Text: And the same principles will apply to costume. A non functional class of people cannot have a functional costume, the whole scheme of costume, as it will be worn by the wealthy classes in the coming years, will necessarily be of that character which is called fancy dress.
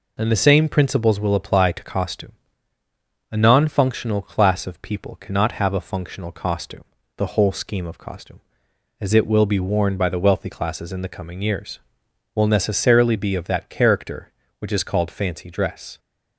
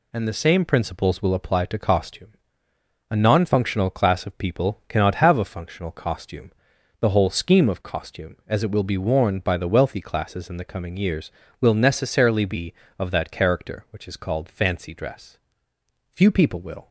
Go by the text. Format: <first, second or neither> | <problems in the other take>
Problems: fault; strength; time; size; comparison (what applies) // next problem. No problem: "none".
first | goes on to say "Few people will"; noticeable; from 16.1 s on; 0.76 s long